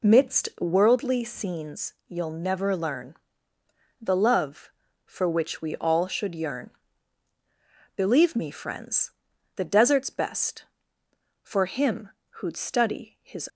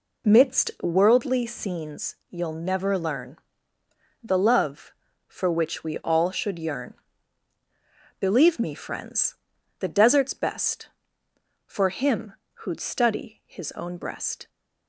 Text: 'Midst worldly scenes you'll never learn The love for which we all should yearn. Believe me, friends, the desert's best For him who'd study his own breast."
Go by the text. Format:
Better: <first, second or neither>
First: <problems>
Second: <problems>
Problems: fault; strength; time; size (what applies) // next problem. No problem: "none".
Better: second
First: pauses between "scenes" and "you'll"; slight; at 1.9 s; 0.16 s long // pauses between "learn" and "The"; noticeable; at 3.1 s; 0.86 s long // pauses between "him" and "who'd"; slight; at 12.0 s; 0.22 s long // stops before "own breast"; at 13.4 s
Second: pauses between "scenes" and "you'll"; slight; at 2.1 s; 0.16 s long // pauses between "learn" and "The"; noticeable; at 3.3 s; 0.86 s long // pauses between "him" and "who'd"; slight; at 12.3 s; 0.22 s long